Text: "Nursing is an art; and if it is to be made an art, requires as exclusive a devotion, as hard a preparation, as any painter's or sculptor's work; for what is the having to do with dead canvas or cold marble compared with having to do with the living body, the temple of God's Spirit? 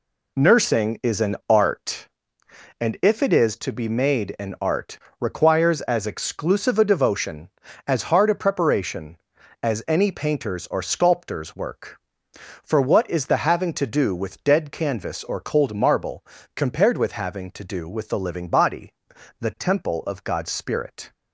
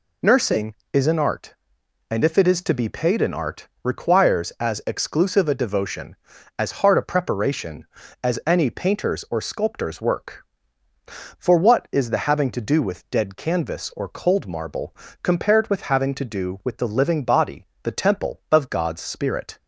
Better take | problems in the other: first | says "paid" for "made"; at 2.8 s // pauses between "marble" and "compared"; slight; at 14.9 s; 0.26 s long; slight in the first

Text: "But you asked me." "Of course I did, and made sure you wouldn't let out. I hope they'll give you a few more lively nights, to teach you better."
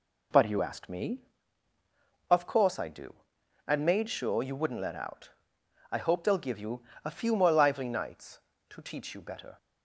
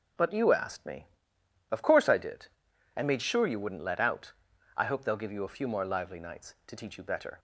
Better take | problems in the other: second | says "do" for "did"; at 2.8 s // pauses between "you" and "a"; slight; at 6.8 s; 0.22 s long

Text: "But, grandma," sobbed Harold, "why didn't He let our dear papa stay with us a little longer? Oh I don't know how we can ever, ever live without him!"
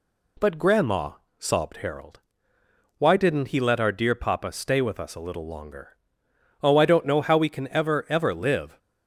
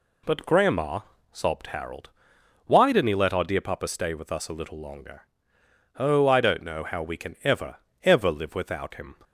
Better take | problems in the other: second | stops before "without him"; at 8.7 s

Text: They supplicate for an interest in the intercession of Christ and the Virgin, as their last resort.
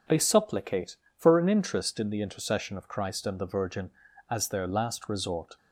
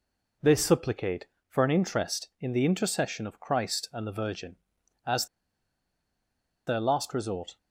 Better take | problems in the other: first | pauses between "as" and "their"; strong; at 5.2 s; 1.4 s long

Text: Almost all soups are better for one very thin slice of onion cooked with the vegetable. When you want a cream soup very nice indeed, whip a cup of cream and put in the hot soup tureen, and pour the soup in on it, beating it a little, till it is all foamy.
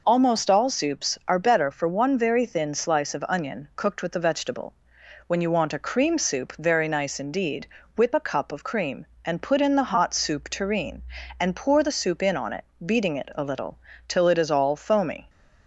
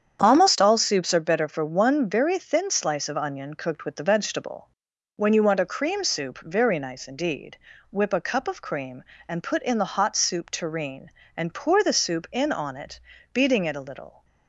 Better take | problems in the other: first | starts louder than the rest; strong; until 1.2 s; 8.5 dB // stops before "till it is all foamy"; at 14.2 s

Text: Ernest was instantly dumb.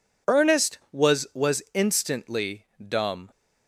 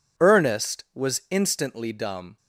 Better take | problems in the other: second | says "was" twice; at 1.3 s // pauses between "instantly" and "dumb"; slight; at 2.6 s; 0.24 s long

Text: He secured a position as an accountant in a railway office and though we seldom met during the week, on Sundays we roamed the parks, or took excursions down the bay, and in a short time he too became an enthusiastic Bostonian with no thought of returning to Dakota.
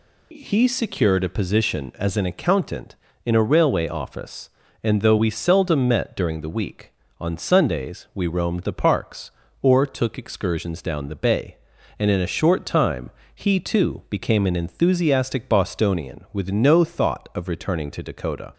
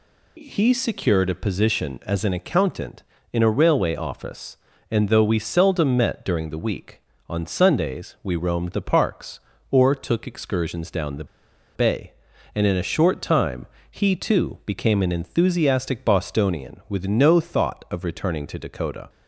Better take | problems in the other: first | pauses between "the" and "bay"; noticeable; at 11.2 s; 0.49 s long // pauses between "time" and "he"; slight; at 13.6 s; 0.26 s long; slight in the first

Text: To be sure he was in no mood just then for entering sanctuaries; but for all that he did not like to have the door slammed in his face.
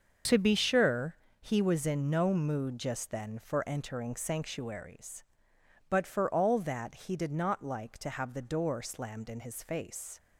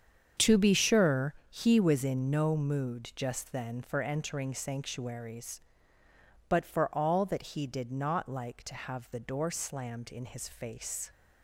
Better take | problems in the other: neither | starts louder than the rest; the same in both // pauses between "sure" and "he"; slight; the same in both

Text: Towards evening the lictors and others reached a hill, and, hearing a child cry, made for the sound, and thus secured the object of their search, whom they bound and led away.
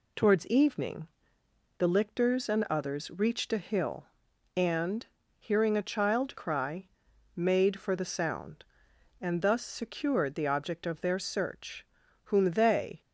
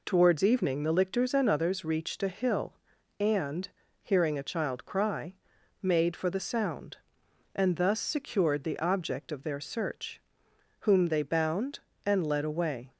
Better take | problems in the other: second | pauses between "evening" and "the"; noticeable; at 1.0 s; 0.72 s long // stops before "bound and led away"; at 13.0 s

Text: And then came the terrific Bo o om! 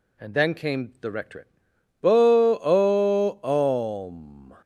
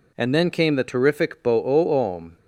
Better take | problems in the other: second | says "rectorate" for "terrific"; at 1.1 s

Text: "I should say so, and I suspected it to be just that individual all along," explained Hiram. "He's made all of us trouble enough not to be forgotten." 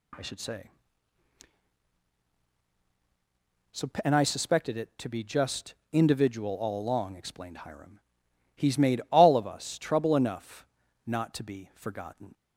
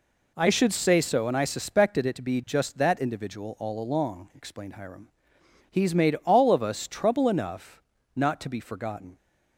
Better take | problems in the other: second | skips "that"; at 5.8 s // pauses between "enough" and "not"; at 10.6 s; 0.40 s long; slight in the second

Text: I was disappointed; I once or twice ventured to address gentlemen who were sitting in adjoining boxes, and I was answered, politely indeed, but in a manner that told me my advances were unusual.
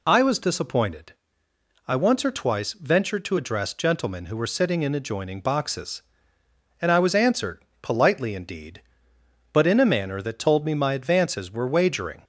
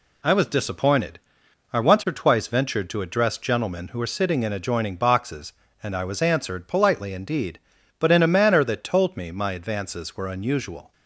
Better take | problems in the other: second | says "wagering" for "unusual"; at 11.6 s

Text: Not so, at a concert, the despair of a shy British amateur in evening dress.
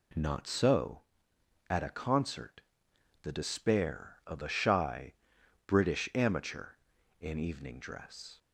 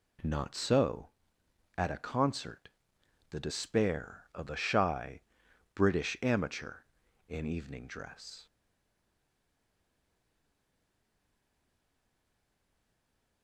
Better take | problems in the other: first | pauses between "shy" and "British"; noticeable; at 5.2 s; 0.52 s long; noticeable in the first // stays silent after the last word; strong; from 8.4 s on; 5.0 s long

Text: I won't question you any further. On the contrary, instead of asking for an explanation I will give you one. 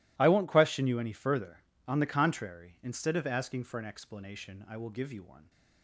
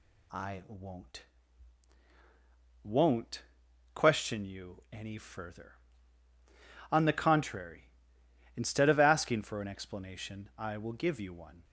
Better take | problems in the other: first | says "won't" twice; at 2.8 s

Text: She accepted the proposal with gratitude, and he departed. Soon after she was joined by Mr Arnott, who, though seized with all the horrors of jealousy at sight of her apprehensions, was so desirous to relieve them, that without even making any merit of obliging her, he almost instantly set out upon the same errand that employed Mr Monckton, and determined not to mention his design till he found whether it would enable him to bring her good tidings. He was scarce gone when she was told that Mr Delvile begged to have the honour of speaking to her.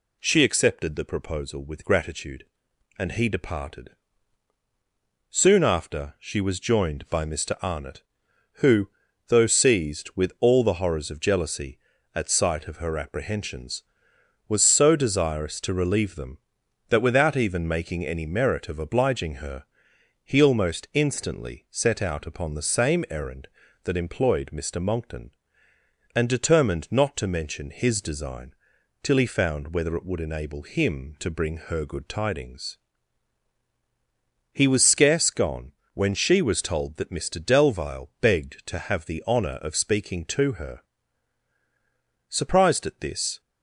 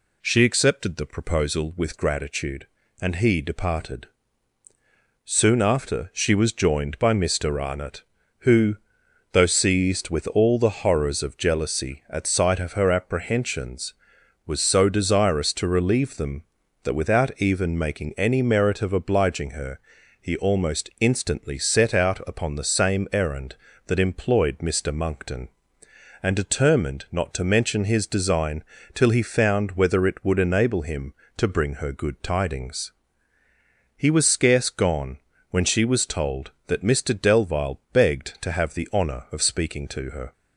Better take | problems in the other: second | pauses between "design" and "till"; noticeable; at 28.5 s; 0.48 s long; slight in the second // pauses between "gone" and "when"; slight; at 35.7 s; 0.24 s long; slight in the second // goes on to say "Surprised at this"; noticeable; from 42.2 s on; 1.1 s long

